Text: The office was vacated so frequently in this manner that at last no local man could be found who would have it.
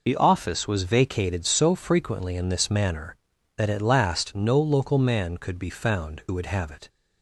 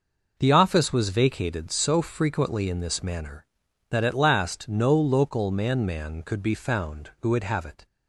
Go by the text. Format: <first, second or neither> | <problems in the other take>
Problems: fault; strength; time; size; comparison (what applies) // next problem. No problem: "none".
first | says "man" twice; at 5.8 s